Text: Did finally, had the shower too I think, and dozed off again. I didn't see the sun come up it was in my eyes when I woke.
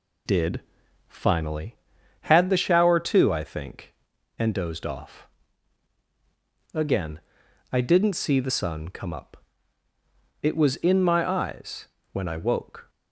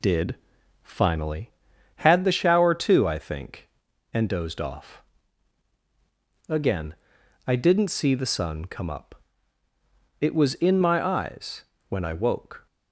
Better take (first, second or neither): neither